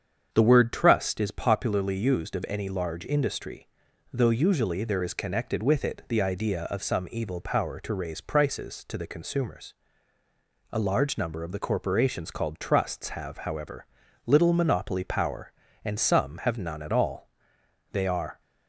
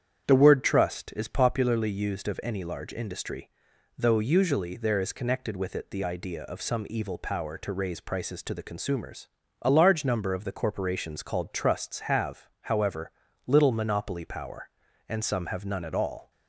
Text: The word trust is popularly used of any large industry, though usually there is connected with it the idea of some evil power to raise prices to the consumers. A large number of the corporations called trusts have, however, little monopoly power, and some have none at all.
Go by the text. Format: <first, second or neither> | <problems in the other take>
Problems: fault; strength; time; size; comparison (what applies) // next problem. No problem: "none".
second | starts louder than the rest; strong; until 1.3 s; 7.5 dB; strong in the second // goes on to say "They are"; slight; from 17.9 s on; 0.48 s long